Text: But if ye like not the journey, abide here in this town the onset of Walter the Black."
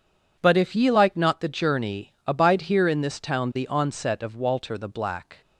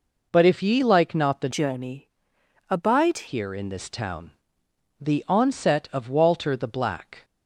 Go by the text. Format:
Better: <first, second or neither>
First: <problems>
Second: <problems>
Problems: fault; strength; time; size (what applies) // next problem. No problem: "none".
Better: first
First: none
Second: changes voice from "journey" to "abide"; from 1.5 to 3.2 s; 1.7 s long // pauses between "town" and "the"; noticeable; at 4.3 s; 0.70 s long